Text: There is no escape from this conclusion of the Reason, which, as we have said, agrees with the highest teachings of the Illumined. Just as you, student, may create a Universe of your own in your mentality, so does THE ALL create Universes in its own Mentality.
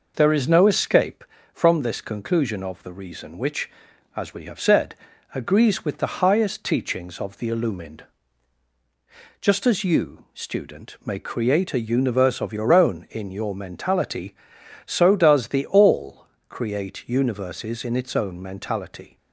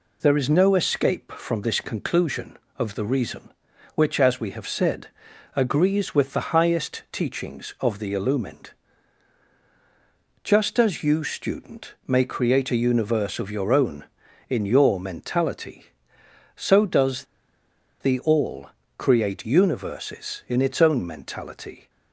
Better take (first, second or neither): first